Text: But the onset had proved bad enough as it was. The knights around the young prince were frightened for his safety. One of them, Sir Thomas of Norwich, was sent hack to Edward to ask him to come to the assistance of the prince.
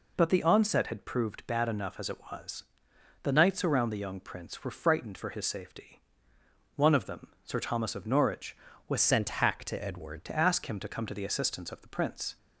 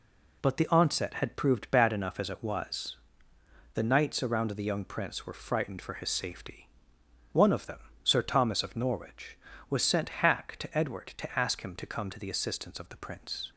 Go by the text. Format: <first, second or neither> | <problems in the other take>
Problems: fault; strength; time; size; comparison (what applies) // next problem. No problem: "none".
second | changes voice from "sent" to "Edward"; from 8.9 to 10.2 s; 1.3 s long